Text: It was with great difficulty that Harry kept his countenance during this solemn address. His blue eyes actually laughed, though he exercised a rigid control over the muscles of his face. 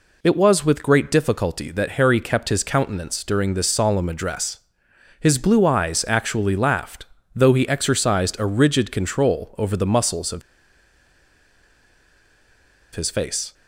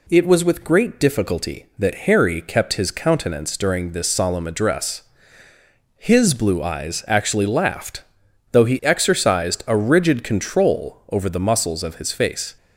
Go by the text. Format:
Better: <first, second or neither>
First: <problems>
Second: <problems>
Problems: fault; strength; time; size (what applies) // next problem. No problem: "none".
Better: second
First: pauses between "of" and "his"; strong; at 10.4 s; 2.5 s long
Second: none